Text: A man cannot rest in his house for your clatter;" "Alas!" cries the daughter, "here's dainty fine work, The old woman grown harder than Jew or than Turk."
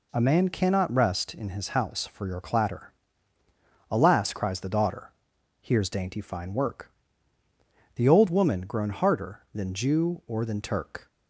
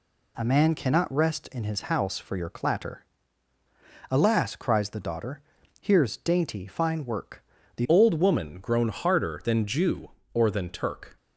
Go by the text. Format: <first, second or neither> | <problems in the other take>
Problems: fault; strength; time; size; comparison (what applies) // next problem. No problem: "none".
first | changes voice at "old"; from 7.8 s on; 3.3 s long